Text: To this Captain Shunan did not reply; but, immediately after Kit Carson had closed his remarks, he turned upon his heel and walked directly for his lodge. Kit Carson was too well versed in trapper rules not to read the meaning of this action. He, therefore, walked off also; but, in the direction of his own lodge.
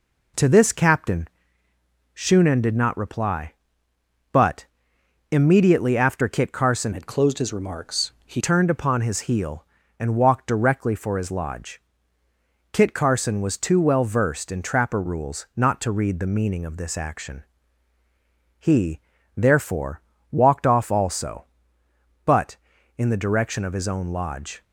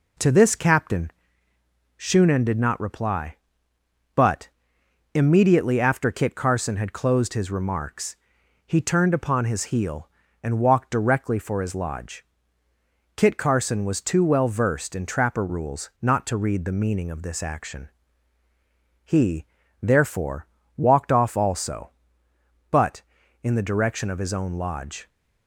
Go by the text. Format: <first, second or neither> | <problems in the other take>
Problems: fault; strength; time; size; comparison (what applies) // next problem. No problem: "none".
second | pauses between "Captain" and "Shunan"; noticeable; at 1.2 s; 0.88 s long; noticeable in the second // changes voice from "had" to "he"; from 6.9 to 8.4 s; 1.5 s long